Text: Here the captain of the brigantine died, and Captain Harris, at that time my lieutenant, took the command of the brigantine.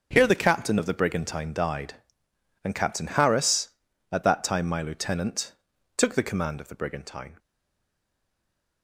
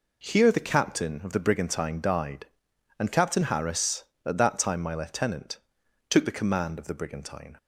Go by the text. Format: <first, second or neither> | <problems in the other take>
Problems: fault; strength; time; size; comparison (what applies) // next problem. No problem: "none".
second | stays silent after the last word; noticeable; from 7.3 s on; 1.5 s long